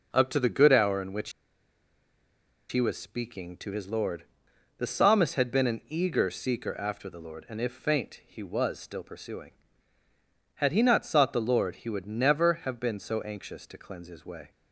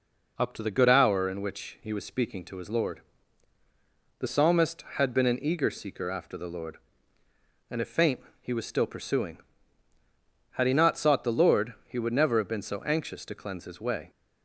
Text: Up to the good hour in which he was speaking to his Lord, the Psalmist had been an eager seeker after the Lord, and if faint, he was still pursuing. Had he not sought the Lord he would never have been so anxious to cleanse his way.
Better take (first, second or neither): second